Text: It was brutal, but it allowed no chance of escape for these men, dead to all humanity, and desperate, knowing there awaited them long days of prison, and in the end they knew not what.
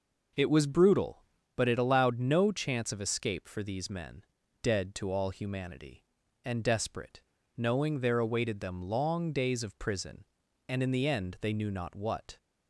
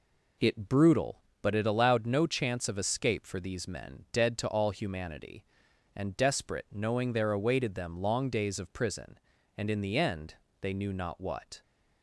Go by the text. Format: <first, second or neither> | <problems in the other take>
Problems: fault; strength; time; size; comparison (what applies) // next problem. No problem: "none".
first | skips "was"; at 0.6 s // pauses between "end" and "they"; slight; at 10.3 s; 0.24 s long